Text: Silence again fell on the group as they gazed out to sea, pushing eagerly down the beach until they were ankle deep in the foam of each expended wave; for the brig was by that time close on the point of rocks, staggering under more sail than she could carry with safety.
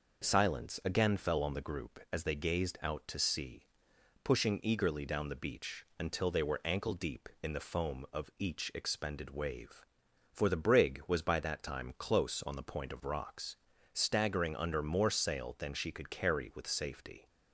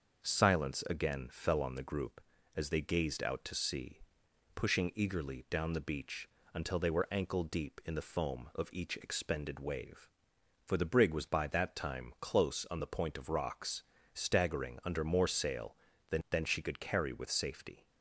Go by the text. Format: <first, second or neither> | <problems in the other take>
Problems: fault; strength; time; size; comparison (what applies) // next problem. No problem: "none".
first | starts louder than the rest; until 1.2 s; 6.5 dB // pauses between "beach" and "until"; slight; at 6.2 s; 0.26 s long // says "than" twice; at 16.2 s